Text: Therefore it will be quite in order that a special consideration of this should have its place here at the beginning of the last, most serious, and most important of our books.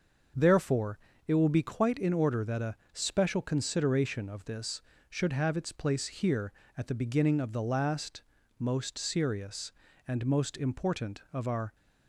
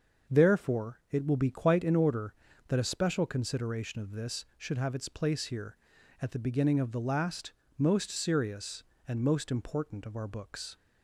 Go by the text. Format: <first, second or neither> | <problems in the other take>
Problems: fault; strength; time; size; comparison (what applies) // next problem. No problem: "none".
second | starts louder than the rest; until 1.6 s; 6.5 dB; also in the second // pauses between "Therefore" and "it"; slight; at 0.9 s; 0.28 s long // pauses between "a" and "special"; slight; at 2.7 s; 0.18 s long // stops before "books"; at 11.7 s